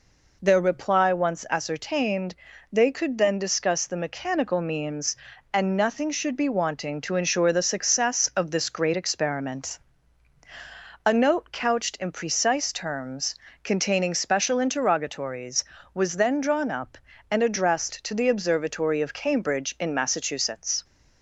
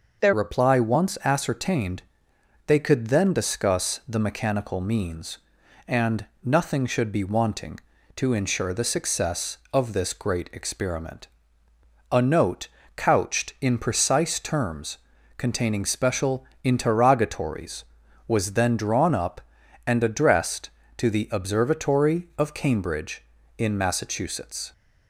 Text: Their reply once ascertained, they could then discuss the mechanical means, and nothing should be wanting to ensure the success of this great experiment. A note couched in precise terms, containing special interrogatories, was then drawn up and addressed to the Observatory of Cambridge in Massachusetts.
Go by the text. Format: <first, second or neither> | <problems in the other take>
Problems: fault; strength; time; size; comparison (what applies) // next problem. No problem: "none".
first | changes voice at "reply"; from 0.3 s on; 24.4 s long // pauses between "and" and "nothing"; slight; at 6.2 s; 0.18 s long // pauses between "note" and "couched"; slight; at 12.6 s; 0.26 s long // pauses between "special" and "interrogatories"; slight; at 16.4 s; 0.18 s long